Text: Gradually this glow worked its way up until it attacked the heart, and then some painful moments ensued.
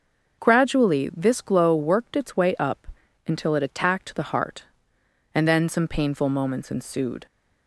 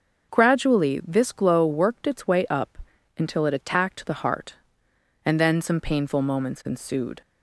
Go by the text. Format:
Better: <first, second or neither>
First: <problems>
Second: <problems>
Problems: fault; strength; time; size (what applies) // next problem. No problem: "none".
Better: neither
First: starts louder than the rest; until 1.4 s; 6.5 dB // pauses between "up" and "until"; at 2.8 s; 0.38 s long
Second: starts louder than the rest; until 1.3 s; 6.5 dB // pauses between "up" and "until"; at 2.7 s; 0.38 s long